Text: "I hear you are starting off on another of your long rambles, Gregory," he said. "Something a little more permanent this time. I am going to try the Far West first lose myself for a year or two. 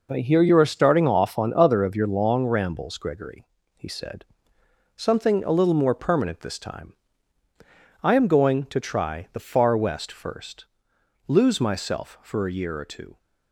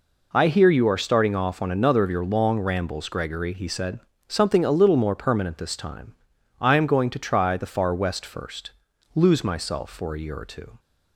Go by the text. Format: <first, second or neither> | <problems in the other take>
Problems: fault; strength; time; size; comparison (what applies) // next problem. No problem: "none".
second | says "other" for "another"; at 1.5 s // pauses between "first" and "lose"; noticeable; at 10.6 s; 0.62 s long; also in the second